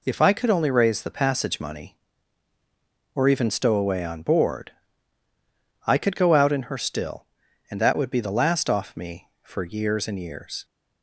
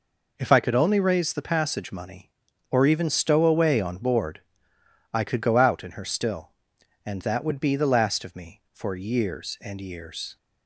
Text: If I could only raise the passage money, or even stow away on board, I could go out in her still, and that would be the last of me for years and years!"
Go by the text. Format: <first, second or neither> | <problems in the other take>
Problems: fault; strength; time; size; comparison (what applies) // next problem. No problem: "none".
second | says "off" for "of"; at 8.6 s